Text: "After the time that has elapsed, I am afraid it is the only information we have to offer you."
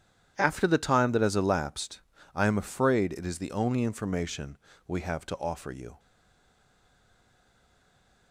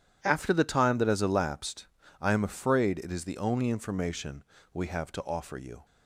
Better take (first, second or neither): second